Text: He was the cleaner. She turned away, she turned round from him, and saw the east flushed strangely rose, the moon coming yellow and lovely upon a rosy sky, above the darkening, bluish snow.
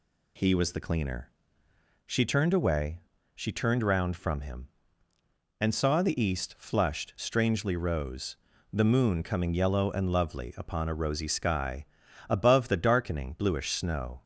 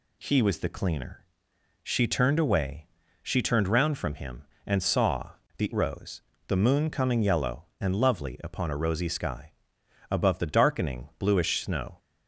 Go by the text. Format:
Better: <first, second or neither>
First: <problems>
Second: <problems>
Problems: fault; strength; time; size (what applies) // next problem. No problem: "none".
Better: first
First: none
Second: pauses between "saw" and "the"; slight; at 5.2 s; 0.26 s long // skips "east flushed strangely"; at 5.7 s